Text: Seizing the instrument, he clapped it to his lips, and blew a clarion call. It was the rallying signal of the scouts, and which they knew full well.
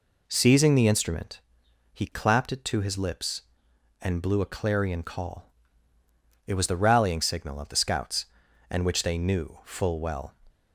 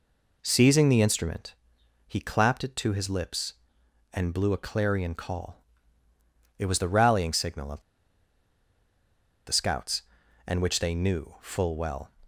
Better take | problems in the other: first | pauses between "of" and "the"; strong; at 7.8 s; 1.6 s long

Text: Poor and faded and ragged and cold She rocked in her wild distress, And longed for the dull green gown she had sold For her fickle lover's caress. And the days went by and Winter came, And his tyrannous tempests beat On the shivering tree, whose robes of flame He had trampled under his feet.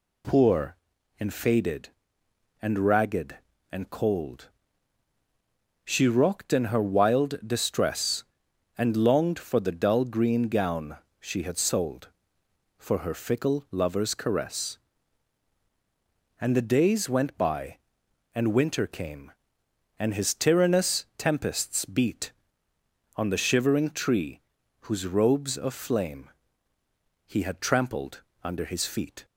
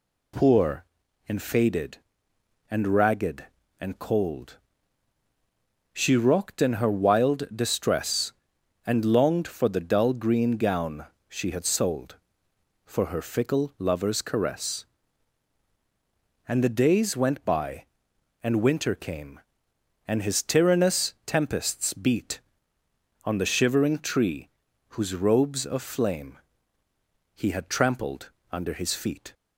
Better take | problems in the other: neither | pauses between "cold" and "She"; strong; the same in both // pauses between "gown" and "she"; slight; the same in both // pauses between "flame" and "He"; noticeable; the same in both // pauses between "trampled" and "under"; slight; the same in both

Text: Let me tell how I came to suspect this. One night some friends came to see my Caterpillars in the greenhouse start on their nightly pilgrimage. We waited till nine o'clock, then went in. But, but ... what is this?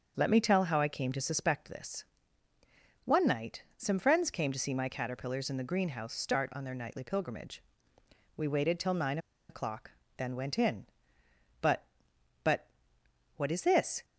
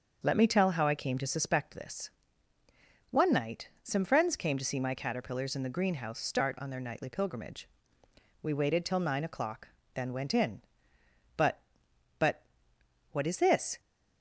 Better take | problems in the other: second | starts louder than the rest; noticeable; until 1.1 s; 6 dB; noticeable in the second // pauses between "nine" and "o'clock"; slight; at 9.1 s; 0.31 s long

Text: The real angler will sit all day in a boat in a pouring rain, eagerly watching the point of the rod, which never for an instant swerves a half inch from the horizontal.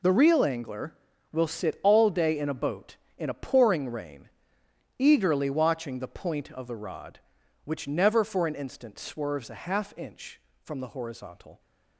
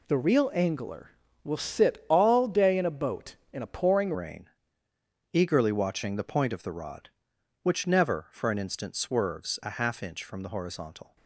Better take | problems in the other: first | changes voice at "rain"; from 4.1 s on; 7.0 s long

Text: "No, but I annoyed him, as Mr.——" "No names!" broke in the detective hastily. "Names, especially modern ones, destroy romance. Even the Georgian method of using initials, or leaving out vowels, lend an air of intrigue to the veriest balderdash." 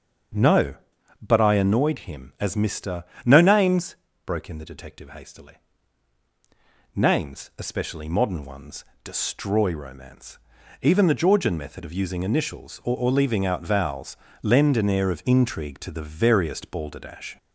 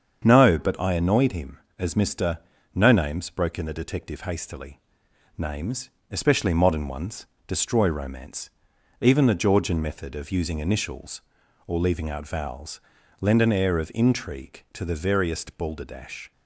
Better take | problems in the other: second | starts louder than the rest; until 1.8 s; 6.5 dB; strong in the second // says "or" twice; at 12.9 s

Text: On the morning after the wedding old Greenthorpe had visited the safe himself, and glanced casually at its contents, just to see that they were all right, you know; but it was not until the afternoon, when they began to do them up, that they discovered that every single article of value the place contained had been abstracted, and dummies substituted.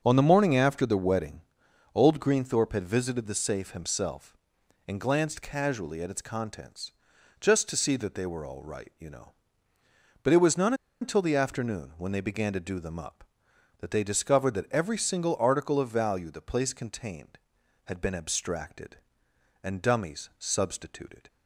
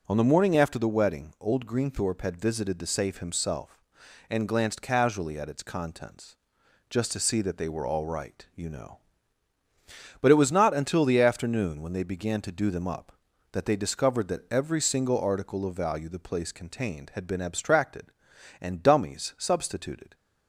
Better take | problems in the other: second | starts louder than the rest; until 1.0 s; 6.5 dB // pauses between "wedding" and "old"; noticeable; at 1.4 s; 0.52 s long // pauses between "not" and "until"; slight; at 10.7 s; 0.27 s long

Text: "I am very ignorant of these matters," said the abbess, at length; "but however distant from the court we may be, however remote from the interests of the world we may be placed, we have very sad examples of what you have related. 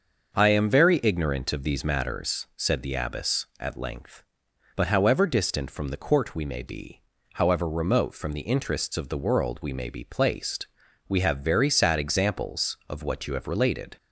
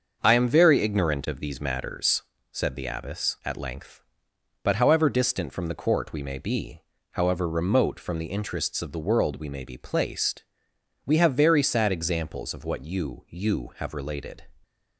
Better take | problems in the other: first | starts louder than the rest; until 1.2 s; 6.5 dB; also in the first // says "you" twice; at 13.2 s

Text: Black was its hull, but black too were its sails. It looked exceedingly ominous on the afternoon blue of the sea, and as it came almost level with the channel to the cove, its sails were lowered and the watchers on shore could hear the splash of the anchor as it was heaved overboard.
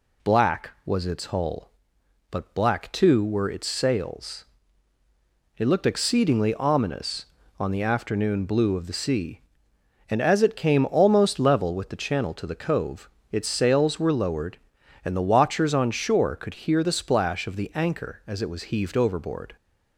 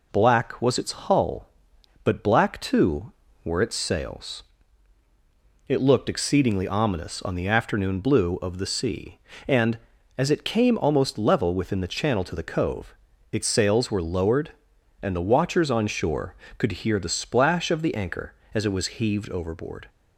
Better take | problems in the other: first | says "within" for "with"; at 11.5 s

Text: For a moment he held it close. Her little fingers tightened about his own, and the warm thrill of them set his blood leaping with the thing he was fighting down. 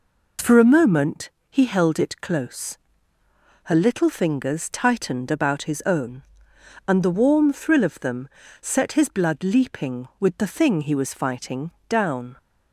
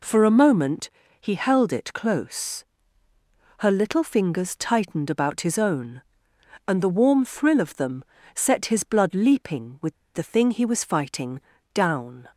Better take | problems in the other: first | pauses between "moment" and "he"; slight; at 0.8 s; 0.32 s long; slight in the first // pauses between "them" and "set"; slight; at 8.0 s; 0.32 s long; slight in the first // pauses between "with" and "the"; slight; at 9.9 s; 0.19 s long // pauses between "fighting" and "down"; slight; at 11.3 s; 0.34 s long; slight in the first

